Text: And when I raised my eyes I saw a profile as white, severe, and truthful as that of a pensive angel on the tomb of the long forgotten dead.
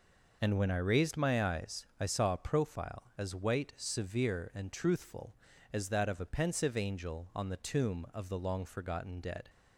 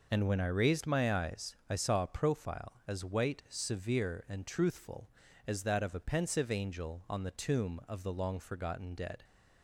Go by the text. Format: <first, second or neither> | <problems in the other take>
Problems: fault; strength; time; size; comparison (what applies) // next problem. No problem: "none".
neither | none